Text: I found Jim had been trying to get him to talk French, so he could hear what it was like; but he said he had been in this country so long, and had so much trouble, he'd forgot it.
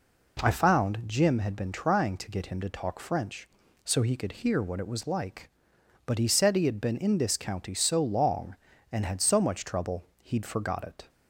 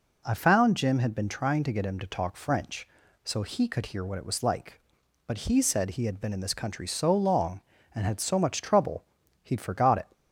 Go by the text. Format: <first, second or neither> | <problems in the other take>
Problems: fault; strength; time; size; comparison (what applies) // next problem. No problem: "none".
second | says "county" for "country"; at 7.3 s